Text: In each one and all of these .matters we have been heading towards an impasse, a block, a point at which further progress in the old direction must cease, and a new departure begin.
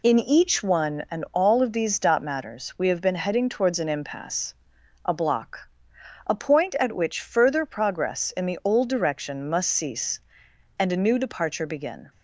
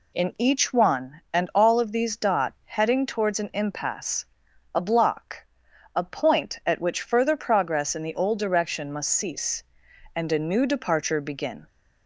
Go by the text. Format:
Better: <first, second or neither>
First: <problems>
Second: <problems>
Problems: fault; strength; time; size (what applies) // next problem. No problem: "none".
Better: first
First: none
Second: skips "matters we have been"; at 2.6 s